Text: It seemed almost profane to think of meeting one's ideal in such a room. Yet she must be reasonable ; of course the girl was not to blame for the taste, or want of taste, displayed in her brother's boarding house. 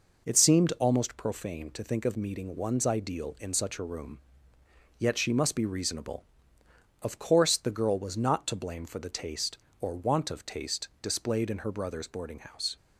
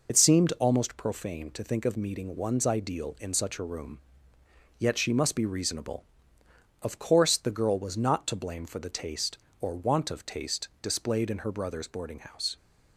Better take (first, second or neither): first